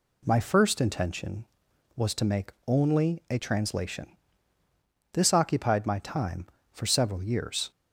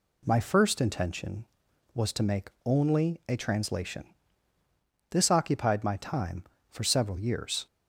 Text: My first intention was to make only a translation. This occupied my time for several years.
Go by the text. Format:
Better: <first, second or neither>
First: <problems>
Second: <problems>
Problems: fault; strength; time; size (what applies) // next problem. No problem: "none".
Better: neither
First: none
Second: none